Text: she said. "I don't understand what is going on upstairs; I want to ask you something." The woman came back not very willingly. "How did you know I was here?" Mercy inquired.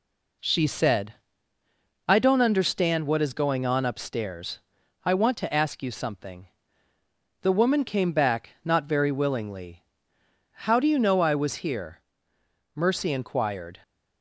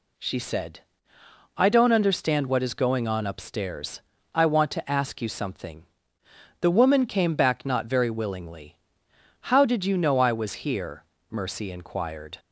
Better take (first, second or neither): second